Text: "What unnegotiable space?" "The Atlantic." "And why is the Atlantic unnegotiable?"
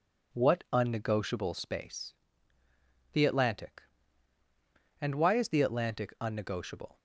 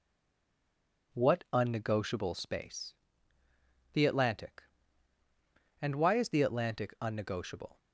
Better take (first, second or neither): first